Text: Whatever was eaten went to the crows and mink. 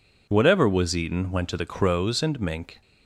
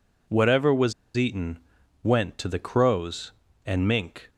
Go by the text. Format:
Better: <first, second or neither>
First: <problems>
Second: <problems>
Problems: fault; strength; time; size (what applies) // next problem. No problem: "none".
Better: first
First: none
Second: pauses between "was" and "eaten"; slight; at 0.9 s; 0.23 s long // pauses between "eaten" and "went"; noticeable; at 1.5 s; 0.46 s long